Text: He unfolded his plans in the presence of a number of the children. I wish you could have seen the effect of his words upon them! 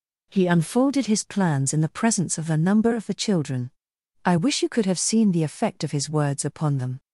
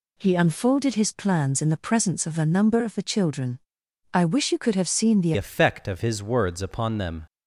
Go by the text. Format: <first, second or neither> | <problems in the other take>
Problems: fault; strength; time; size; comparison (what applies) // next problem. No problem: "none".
first | changes voice at "effect"; from 5.3 s on; 1.9 s long